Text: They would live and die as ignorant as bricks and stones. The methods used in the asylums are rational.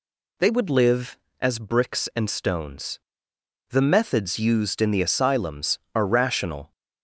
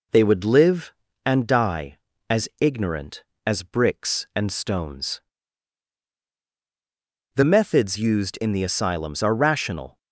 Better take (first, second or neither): second